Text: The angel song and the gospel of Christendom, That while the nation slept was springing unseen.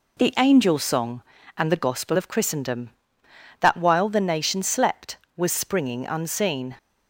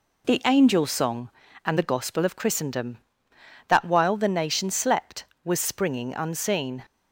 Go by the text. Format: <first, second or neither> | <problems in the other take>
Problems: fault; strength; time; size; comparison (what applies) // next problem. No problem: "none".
neither | none